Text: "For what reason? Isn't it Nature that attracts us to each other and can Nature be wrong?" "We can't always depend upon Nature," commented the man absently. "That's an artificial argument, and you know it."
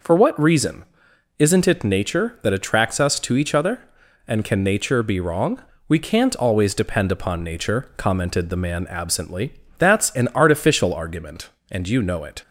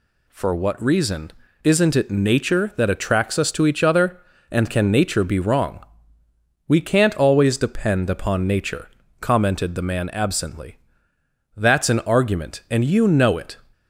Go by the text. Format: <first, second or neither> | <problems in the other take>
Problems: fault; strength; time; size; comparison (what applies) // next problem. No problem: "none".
first | skips "artificial"; at 12.0 s